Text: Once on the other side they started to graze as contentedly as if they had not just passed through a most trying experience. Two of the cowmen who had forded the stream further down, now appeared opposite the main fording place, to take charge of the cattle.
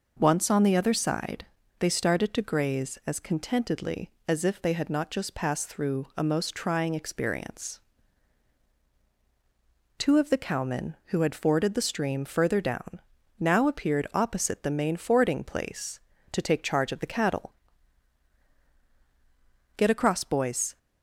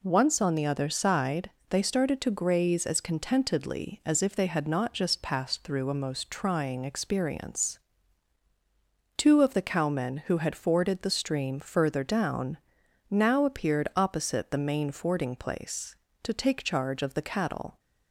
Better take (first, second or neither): second